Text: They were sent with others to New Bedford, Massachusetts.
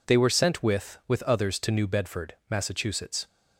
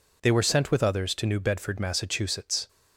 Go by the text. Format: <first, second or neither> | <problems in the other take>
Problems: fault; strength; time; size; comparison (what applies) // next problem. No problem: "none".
second | says "with" twice; at 1.0 s